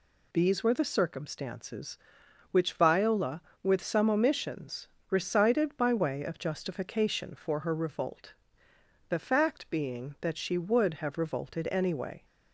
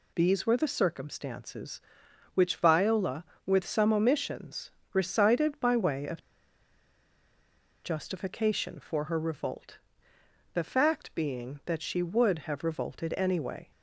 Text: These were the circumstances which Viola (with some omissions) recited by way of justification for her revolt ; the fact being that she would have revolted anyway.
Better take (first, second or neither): first